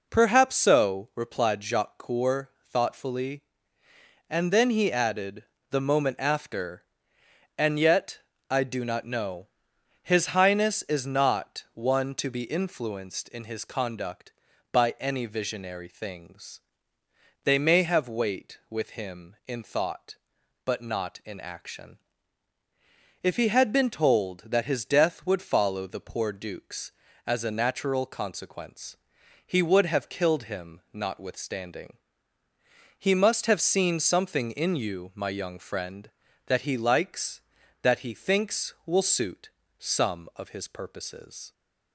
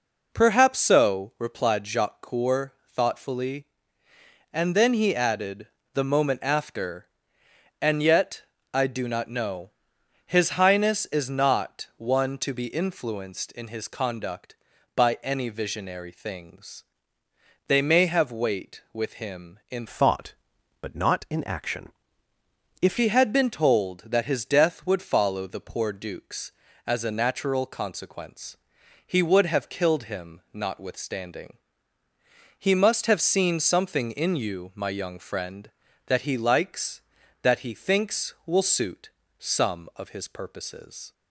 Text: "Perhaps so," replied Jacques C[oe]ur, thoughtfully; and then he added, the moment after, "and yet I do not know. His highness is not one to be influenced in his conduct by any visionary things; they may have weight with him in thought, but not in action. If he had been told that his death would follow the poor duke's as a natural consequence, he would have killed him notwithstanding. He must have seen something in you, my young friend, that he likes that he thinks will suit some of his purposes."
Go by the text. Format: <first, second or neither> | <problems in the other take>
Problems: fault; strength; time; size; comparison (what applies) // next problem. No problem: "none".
first | pauses between "yet" and "I"; slight; at 8.4 s; 0.30 s long; slight in the first // changes voice from "thought" to "If"; from 19.8 to 22.9 s; 3.1 s long // pauses between "suit" and "some"; slight; at 39.1 s; 0.28 s long; slight in the first